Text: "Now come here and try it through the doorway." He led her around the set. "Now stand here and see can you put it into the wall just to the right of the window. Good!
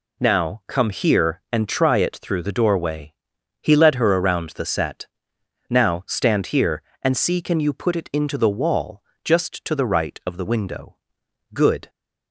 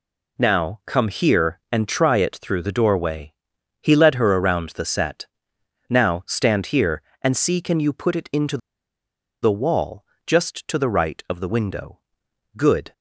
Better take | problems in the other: first | pauses between "into" and "the"; noticeable; at 8.5 s; 0.84 s long // pauses between "wall" and "just"; slight; at 10.0 s; 0.22 s long; slight in the first

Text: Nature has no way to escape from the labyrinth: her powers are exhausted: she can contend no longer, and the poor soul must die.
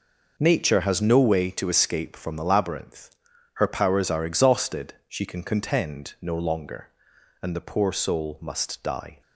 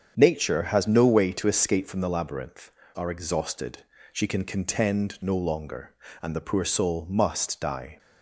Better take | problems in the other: first | starts louder than the rest; strong; until 1.1 s; 8 dB // skips "her powers"; at 2.8 s

